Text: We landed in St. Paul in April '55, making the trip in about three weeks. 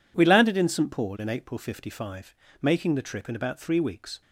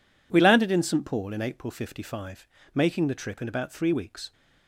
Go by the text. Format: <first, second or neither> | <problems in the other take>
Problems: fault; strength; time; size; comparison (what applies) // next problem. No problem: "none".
neither | none